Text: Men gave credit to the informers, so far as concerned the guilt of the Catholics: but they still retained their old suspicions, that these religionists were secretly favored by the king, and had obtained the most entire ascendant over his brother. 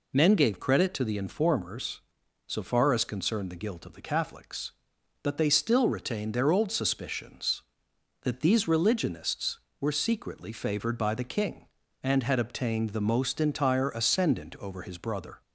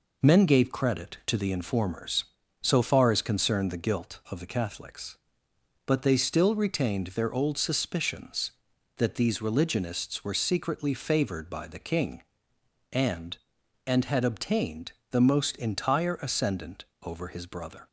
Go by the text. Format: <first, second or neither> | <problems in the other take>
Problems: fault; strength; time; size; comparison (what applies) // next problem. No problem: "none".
first | says "and" twice; at 13.8 s // pauses between "obtained" and "the"; slight; at 14.9 s; 0.20 s long // pauses between "ascendant" and "over"; slight; at 16.8 s; 0.18 s long